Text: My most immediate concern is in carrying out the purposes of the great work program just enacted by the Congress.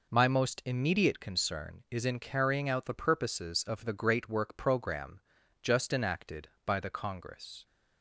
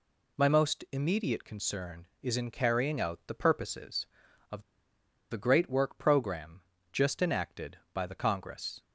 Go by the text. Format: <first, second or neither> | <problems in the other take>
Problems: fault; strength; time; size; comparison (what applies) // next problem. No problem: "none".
first | pauses between "of" and "the"; noticeable; at 4.6 s; 0.68 s long // pauses between "program" and "just"; slight; at 6.6 s; 0.30 s long; also in the first